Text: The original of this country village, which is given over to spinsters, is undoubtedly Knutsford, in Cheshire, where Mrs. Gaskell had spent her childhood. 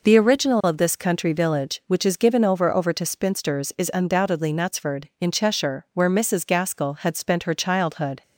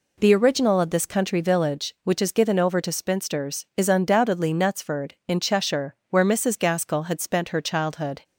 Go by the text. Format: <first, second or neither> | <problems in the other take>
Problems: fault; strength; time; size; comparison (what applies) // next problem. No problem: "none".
second | says "over" twice; at 2.7 s